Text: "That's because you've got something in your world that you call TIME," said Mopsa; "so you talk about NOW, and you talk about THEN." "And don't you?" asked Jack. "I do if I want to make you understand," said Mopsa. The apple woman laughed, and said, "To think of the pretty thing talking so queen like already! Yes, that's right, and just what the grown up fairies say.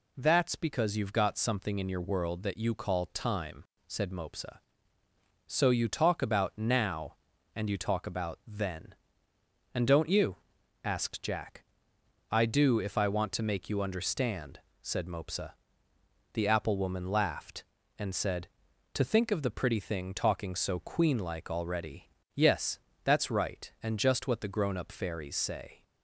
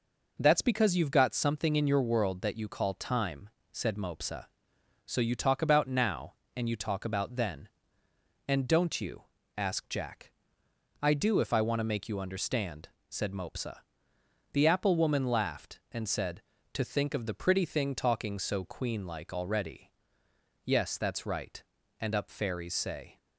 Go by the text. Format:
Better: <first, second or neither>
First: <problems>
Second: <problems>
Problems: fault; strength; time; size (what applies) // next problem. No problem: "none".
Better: first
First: none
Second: skips "just what the grown"; at 22.1 s